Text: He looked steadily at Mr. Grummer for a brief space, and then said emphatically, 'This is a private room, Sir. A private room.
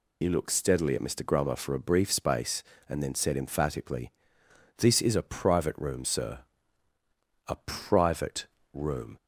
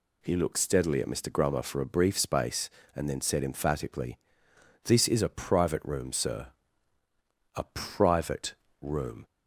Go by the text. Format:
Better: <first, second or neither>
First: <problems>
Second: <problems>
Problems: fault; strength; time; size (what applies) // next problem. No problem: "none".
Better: second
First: loses the start of "He"; at 0.2 s; 60 ms // pauses between "private" and "room"; slight; at 8.4 s; 0.30 s long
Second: pauses between "private" and "room"; slight; at 8.5 s; 0.30 s long